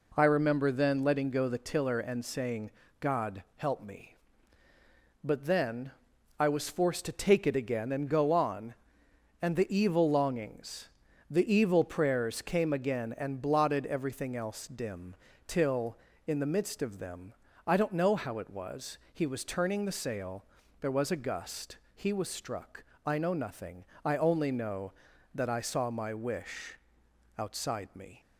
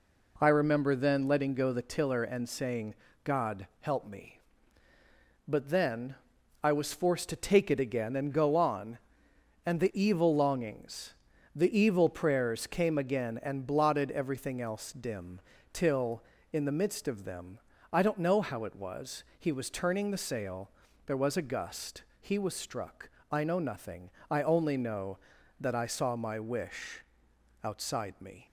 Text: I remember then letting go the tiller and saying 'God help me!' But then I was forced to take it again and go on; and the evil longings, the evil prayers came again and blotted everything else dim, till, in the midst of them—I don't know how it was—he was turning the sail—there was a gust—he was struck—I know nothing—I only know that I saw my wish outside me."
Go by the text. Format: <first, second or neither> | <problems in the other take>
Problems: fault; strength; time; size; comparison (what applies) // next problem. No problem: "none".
neither | pauses between "saying" and "God"; slight; the same in both // pauses between "then" and "I"; noticeable; the same in both // pauses between "wish" and "outside"; noticeable; the same in both